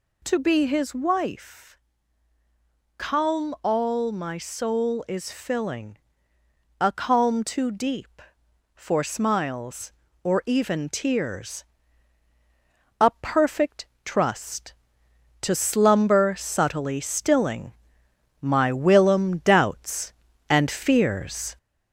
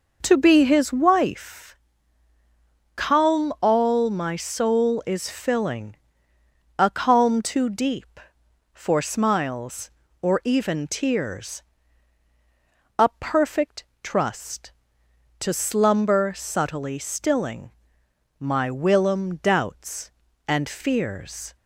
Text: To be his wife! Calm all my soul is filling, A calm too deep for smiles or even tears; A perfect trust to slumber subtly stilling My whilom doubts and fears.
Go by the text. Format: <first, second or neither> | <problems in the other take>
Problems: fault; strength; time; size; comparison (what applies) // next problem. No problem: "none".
second | gets louder; slight; throughout; 2.5 dB // pauses between "perfect" and "trust"; slight; at 13.8 s; 0.20 s long; slight in the second // pauses between "stilling" and "My"; noticeable; at 17.7 s; 0.68 s long; noticeable in the second